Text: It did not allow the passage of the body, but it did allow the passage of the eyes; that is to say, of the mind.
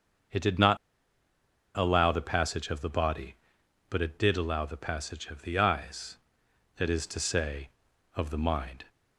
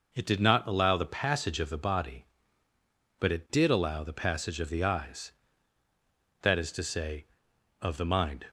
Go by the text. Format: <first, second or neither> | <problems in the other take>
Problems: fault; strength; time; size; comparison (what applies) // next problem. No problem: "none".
second | starts louder than the rest; until 2.3 s; 6.5 dB // pauses between "not" and "allow"; at 0.7 s; 1.0 s long